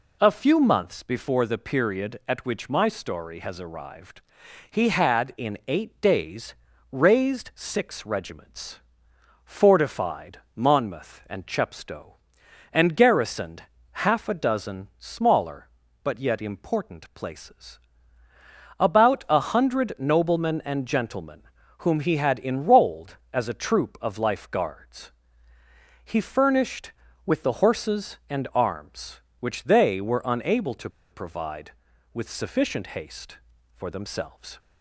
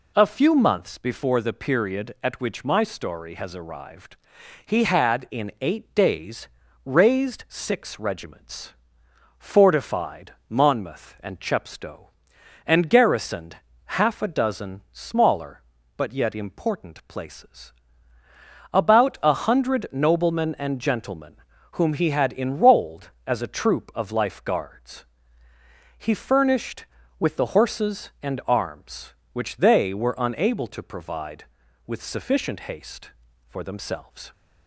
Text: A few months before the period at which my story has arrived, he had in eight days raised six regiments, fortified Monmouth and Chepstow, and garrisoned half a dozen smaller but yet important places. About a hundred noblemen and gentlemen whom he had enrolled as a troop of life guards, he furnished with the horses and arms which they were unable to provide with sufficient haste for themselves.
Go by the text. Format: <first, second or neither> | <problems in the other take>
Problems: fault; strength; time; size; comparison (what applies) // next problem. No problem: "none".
second | pauses between "days" and "raised"; slight; at 6.5 s; 0.36 s long; slight in the second // pauses between "fortified" and "Monmouth"; slight; at 10.3 s; 0.16 s long; slight in the second // pauses between "garrisoned" and "half"; at 13.6 s; 0.42 s long; also in the second // pauses between "gentlemen" and "whom"; slight; at 21.4 s; 0.36 s long; slight in the second // pauses between "to" and "provide"; slight; at 30.8 s; 0.22 s long